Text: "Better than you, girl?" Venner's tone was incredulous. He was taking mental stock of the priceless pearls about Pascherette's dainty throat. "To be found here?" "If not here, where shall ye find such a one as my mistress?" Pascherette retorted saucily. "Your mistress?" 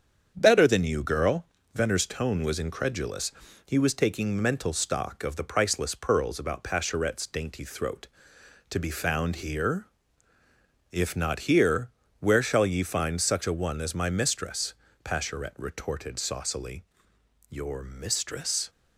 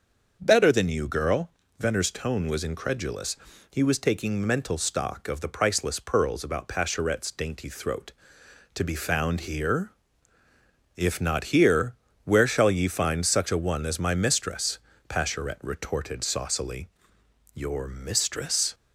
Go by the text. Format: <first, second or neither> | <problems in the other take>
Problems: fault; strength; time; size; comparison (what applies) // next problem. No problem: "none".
second | gets quieter; throughout; 3.5 dB // starts louder than the rest; strong; until 1.3 s; 7.5 dB; also in the second